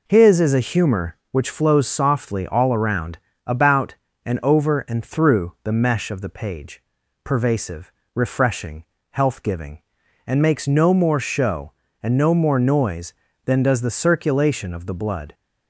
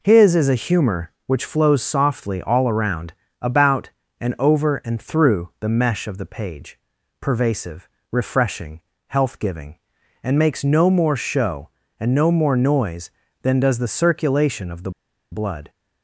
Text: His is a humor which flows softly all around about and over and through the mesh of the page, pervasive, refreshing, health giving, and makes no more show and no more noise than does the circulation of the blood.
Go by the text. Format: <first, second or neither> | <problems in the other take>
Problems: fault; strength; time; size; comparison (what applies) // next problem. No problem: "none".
first | pauses between "around" and "about"; slight; at 3.1 s; 0.28 s long; slight in the first // pauses between "the" and "blood"; at 14.9 s; 0.41 s long